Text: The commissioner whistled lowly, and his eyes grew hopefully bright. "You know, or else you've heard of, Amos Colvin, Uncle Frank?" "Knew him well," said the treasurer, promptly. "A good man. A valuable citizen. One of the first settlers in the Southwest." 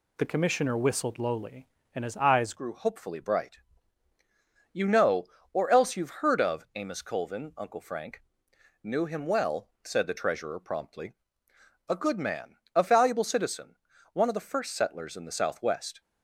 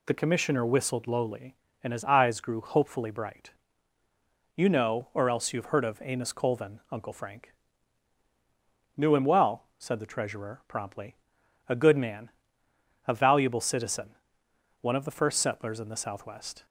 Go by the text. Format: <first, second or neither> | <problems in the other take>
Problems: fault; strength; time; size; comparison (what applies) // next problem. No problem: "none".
second | changes voice at "grew"; from 2.5 s on; 13.5 s long